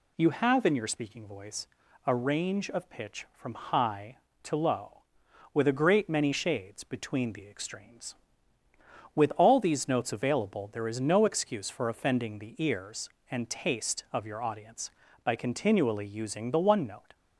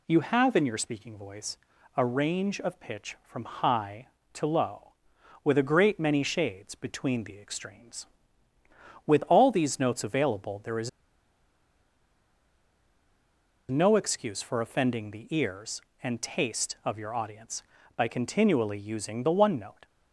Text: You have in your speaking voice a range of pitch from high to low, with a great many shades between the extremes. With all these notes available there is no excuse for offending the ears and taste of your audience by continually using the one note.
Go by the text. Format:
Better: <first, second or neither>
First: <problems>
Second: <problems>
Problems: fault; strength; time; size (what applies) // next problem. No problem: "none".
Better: first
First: pauses between "voice" and "a"; at 1.6 s; 0.38 s long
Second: pauses between "voice" and "a"; at 1.5 s; 0.38 s long // pauses between "is" and "no"; strong; at 10.8 s; 2.8 s long